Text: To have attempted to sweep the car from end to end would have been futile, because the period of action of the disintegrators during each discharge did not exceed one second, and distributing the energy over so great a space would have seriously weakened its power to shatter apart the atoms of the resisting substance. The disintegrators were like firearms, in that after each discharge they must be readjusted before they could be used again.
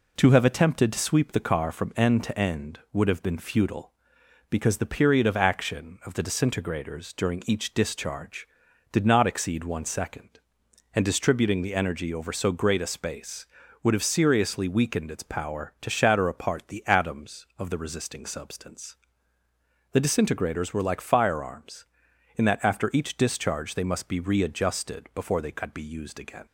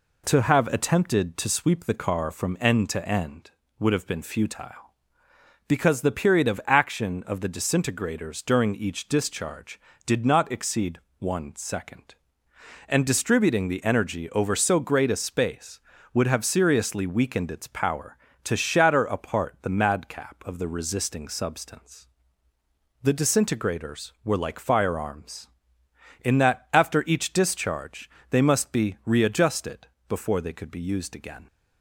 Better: first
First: none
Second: pauses between "exceed" and "one"; slight; at 10.9 s; 0.20 s long // says "madcap" for "atoms"; at 19.7 s // pauses between "discharge" and "they"; slight; at 28.0 s; 0.22 s long // pauses between "readjusted" and "before"; slight; at 29.8 s; 0.20 s long

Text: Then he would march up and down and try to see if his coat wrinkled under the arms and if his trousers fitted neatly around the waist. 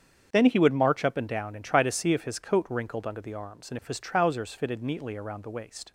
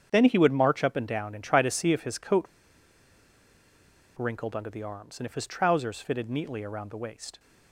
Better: first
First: starts louder than the rest; strong; until 1.3 s; 7.5 dB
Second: starts louder than the rest; strong; until 1.1 s; 7.5 dB // pauses between "coat" and "wrinkled"; strong; at 2.4 s; 1.7 s long

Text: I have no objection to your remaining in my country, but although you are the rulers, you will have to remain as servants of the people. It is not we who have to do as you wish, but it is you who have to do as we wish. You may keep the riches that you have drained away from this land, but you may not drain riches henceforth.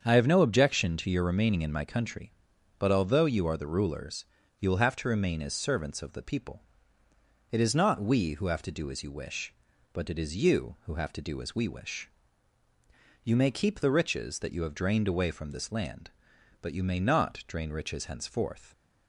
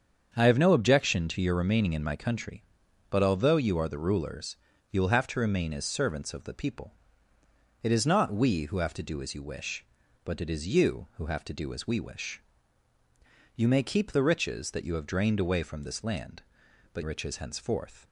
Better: first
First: starts louder than the rest; strong; until 1.0 s; 7 dB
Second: starts louder than the rest; strong; until 1.3 s; 7 dB // skips "you may not drain"; at 17.0 s

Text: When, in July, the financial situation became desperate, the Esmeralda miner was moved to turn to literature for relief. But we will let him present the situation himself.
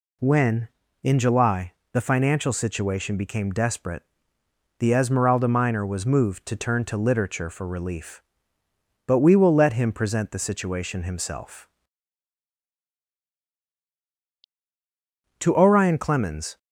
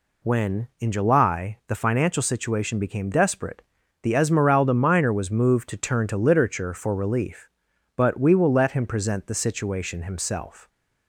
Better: second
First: goes on to say "To Orion Clemens"; noticeable; from 15.3 s on; 1.1 s long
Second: none

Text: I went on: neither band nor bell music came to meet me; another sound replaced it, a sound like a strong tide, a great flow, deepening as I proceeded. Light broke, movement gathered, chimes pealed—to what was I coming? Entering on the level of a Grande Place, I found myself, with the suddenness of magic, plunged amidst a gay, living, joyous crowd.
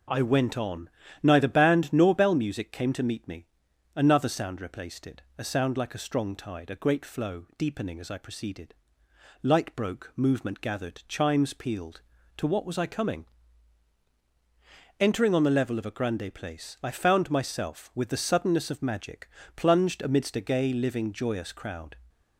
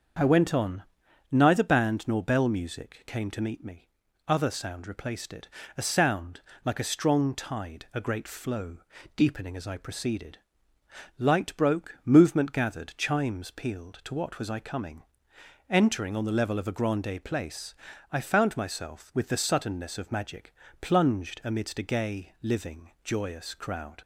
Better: first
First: none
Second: starts louder than the rest; until 1.6 s; 6.5 dB // says "other" for "another"; at 4.2 s // pauses between "sound" and "like"; slight; at 6.4 s; 0.24 s long

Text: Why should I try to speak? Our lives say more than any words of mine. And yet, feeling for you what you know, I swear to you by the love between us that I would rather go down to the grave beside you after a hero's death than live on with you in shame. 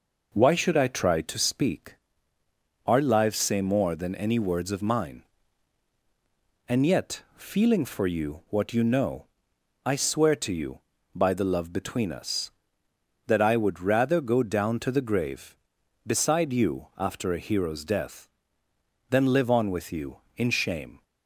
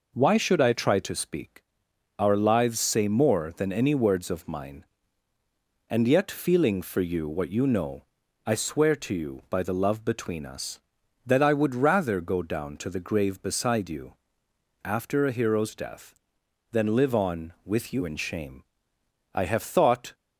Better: first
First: none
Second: pauses between "you" and "after"; noticeable; at 14.1 s; 0.70 s long // goes on to say "I have thought"; noticeable; from 19.3 s on; 0.80 s long

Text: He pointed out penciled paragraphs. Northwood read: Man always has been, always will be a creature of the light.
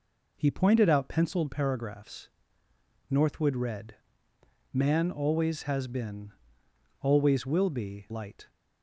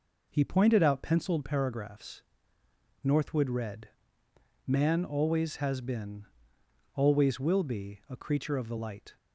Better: second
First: skips "a creature of the"; at 8.0 s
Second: none

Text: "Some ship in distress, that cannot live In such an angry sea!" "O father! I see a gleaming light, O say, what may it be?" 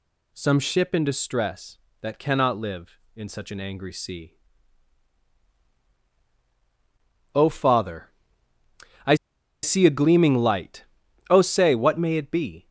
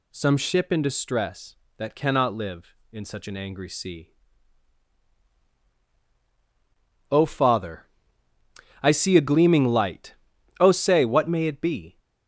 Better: second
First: pauses between "I" and "see"; noticeable; at 9.1 s; 0.48 s long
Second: none

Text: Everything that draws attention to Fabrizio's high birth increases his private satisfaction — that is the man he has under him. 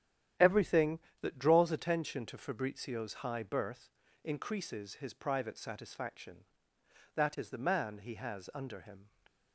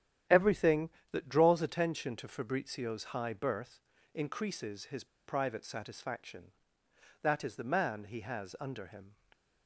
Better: first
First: starts louder than the rest; strong; until 1.6 s; 10.5 dB // pauses between "birth" and "increases"; slight; at 3.8 s; 0.34 s long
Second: starts louder than the rest; strong; until 1.5 s; 10.5 dB // pauses between "birth" and "increases"; slight; at 3.7 s; 0.34 s long // pauses between "his" and "private"; slight; at 5.0 s; 0.19 s long

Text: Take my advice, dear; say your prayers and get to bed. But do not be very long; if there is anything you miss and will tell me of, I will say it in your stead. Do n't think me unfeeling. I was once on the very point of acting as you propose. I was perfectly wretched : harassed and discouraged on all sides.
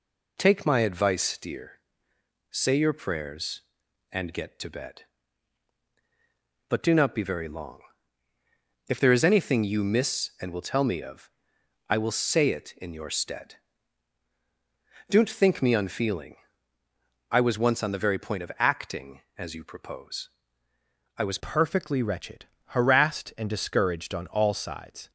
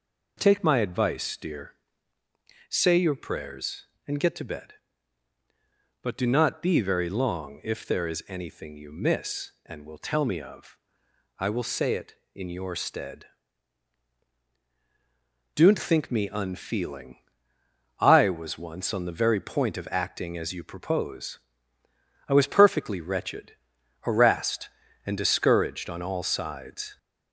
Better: second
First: changes voice at "perfectly"; from 21.3 s on; 3.8 s long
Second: none

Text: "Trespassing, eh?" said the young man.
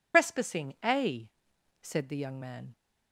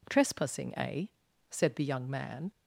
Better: second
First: loses the start of "Trespassing"; at 0.1 s; 115 ms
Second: none

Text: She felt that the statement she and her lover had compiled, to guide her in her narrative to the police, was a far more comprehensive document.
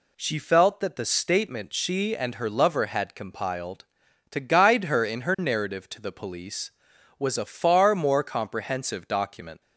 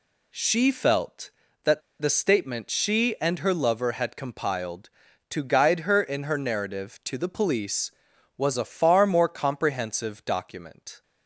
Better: first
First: none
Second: pauses between "that" and "the"; slight; at 1.8 s; 0.20 s long

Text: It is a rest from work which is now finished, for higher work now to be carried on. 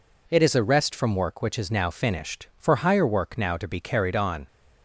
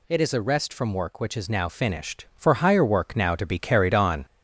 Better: first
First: none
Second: gets louder; noticeable; throughout; 4.5 dB

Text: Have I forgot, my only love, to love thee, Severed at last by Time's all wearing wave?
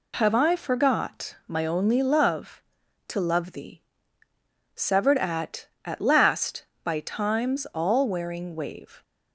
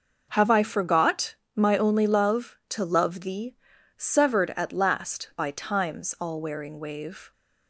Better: second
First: says "at" twice; at 5.8 s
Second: none

